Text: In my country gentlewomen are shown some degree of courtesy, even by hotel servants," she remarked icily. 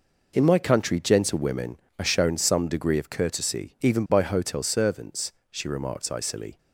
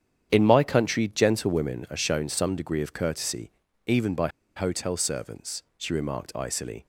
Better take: first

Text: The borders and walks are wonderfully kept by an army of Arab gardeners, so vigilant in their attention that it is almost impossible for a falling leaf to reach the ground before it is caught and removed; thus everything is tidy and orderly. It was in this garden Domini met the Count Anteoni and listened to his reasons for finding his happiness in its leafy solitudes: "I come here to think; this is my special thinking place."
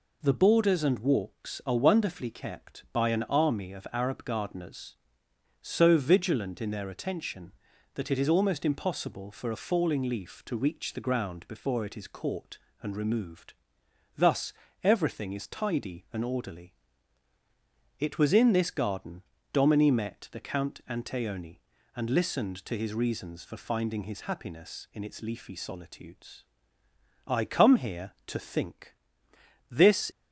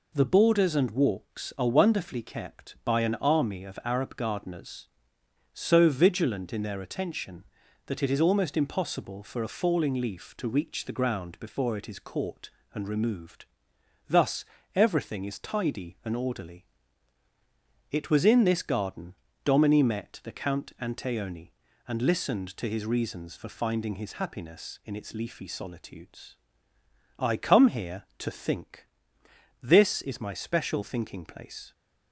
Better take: second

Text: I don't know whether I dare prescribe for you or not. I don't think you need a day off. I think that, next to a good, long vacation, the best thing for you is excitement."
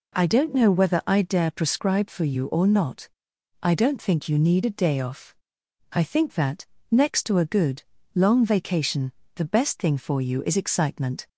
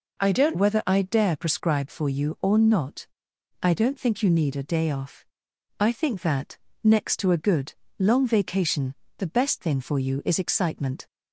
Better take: first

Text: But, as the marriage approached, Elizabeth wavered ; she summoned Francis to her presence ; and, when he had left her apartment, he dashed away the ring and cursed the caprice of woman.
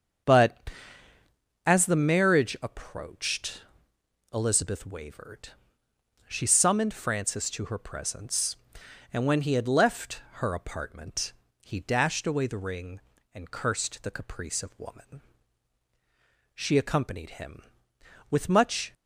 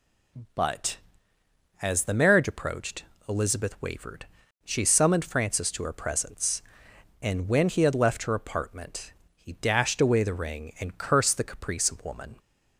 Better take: second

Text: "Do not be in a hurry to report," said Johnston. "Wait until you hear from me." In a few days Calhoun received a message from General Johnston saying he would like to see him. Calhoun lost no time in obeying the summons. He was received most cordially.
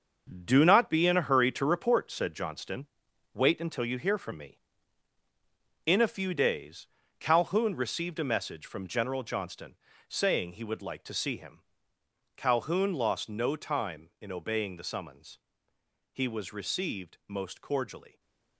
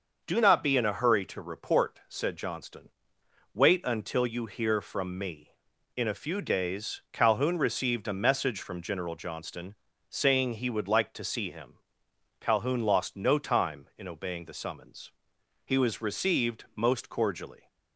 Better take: second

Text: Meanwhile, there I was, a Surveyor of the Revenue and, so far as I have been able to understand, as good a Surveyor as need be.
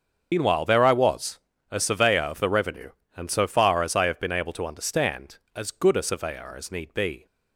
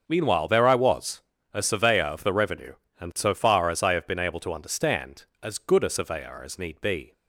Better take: second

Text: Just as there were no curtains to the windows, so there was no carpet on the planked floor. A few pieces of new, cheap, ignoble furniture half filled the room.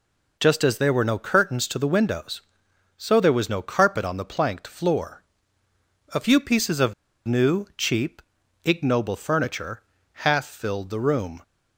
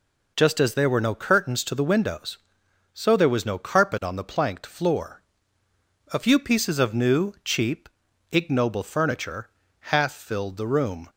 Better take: second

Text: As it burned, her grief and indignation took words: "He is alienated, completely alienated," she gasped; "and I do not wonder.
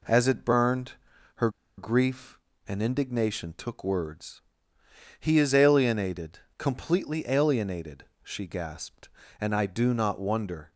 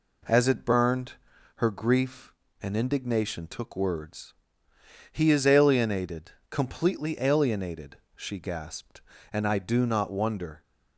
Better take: second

